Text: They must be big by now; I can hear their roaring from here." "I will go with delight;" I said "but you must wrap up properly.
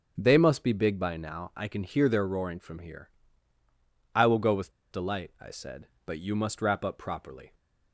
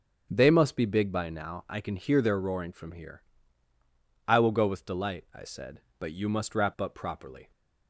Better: second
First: starts louder than the rest; until 1.1 s; 6.5 dB // pauses between "with" and "delight"; slight; at 4.7 s; 0.20 s long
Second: starts louder than the rest; until 1.3 s; 6.5 dB

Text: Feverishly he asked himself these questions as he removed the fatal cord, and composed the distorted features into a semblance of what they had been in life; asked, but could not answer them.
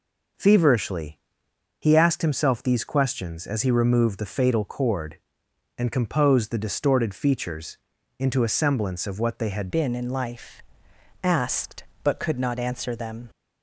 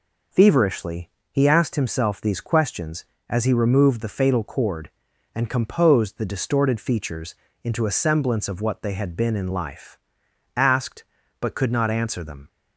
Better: second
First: pauses between "Feverishly" and "he"; noticeable; at 1.1 s; 0.60 s long // pauses between "features" and "into"; at 7.7 s; 0.42 s long // changes voice at "been"; from 9.7 s on; 3.5 s long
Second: pauses between "Feverishly" and "he"; slight; at 1.1 s; 0.20 s long // pauses between "features" and "into"; slight; at 7.3 s; 0.28 s long

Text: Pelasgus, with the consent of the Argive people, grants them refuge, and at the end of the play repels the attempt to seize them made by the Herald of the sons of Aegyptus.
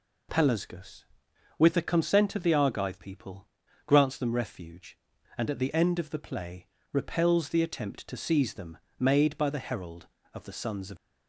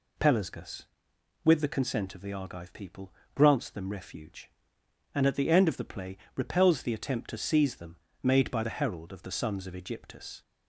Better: second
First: pauses between "play" and "repels"; slight; at 6.6 s; 0.26 s long // pauses between "them" and "made"; slight; at 8.7 s; 0.22 s long // stops before "Aegyptus"; at 10.9 s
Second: pauses between "play" and "repels"; slight; at 6.1 s; 0.20 s long // pauses between "them" and "made"; slight; at 7.9 s; 0.26 s long

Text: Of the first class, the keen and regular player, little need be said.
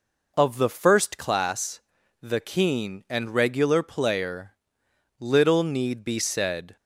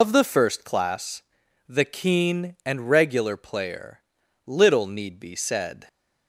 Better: first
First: none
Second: loses the start of "Of"; at 0.0 s; 80 ms

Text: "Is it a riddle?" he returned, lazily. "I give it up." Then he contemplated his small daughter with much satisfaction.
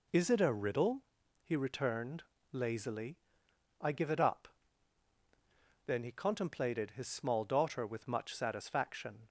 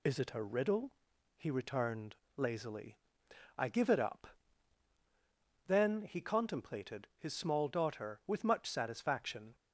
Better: neither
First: none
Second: none

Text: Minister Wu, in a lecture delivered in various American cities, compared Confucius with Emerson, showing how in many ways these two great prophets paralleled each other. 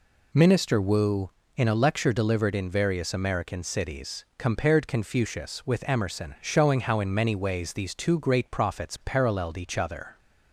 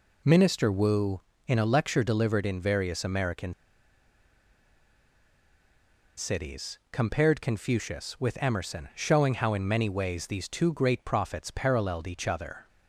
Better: first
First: none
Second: pauses between "American" and "cities"; strong; at 3.5 s; 2.6 s long

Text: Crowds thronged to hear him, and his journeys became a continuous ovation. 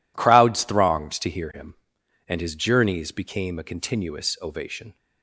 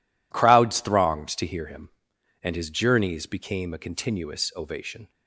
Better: neither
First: none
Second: none

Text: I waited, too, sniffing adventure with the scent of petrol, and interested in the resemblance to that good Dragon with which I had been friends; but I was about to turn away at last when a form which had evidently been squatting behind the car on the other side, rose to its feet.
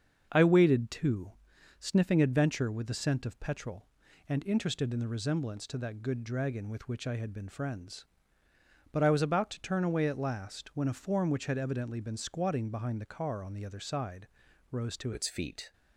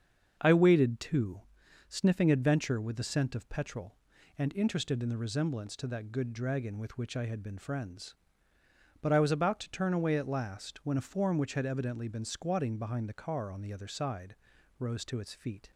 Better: second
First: starts louder than the rest; until 1.3 s; 7 dB // changes voice at "its"; from 15.1 s on; 0.6 s long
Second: starts louder than the rest; until 1.4 s; 7 dB

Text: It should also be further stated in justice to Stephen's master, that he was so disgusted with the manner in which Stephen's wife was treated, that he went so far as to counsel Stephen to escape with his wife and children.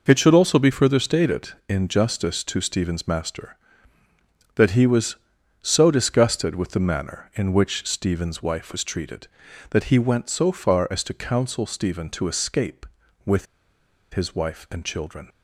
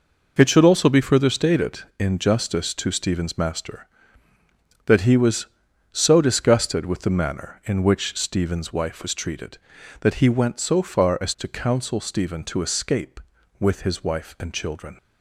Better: second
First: pauses between "with" and "his"; noticeable; at 13.4 s; 0.68 s long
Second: none

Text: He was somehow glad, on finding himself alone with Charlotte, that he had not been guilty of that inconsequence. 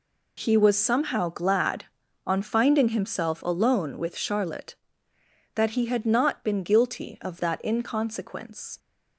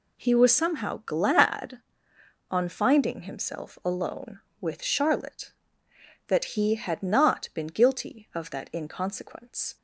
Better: neither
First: none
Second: none

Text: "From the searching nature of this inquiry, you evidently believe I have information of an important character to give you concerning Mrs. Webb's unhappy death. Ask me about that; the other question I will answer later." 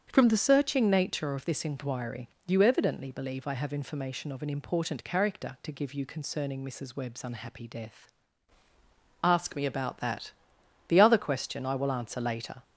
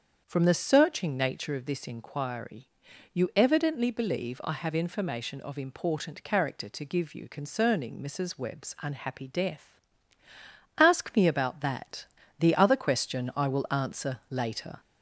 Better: first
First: starts louder than the rest; strong; until 1.1 s; 7.5 dB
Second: starts louder than the rest; strong; until 1.2 s; 7.5 dB // skips "an"; at 5.5 s

